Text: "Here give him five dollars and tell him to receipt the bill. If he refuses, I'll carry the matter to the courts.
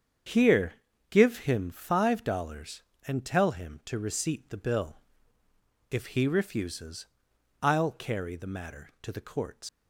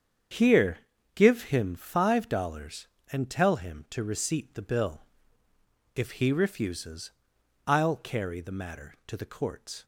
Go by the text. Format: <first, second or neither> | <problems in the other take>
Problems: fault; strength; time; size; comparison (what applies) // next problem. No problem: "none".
second | starts louder than the rest; strong; until 1.6 s; 7.5 dB; strong in the second // pauses between "Here" and "give"; slight; at 0.7 s; 0.36 s long; slight in the second // leaves "courts" unfinished; at 9.6 s; 100 ms